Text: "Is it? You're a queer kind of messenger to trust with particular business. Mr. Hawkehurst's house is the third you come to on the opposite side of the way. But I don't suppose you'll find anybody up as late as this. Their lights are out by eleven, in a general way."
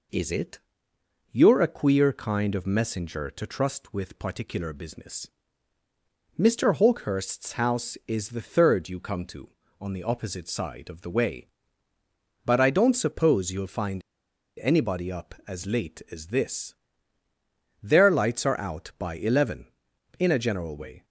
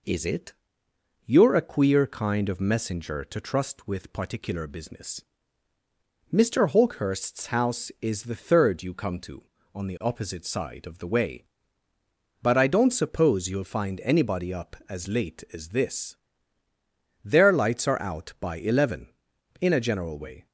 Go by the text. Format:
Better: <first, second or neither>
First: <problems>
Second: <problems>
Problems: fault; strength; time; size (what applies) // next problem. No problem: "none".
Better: second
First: pauses between "find" and "anybody"; noticeable; at 14.0 s; 0.61 s long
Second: none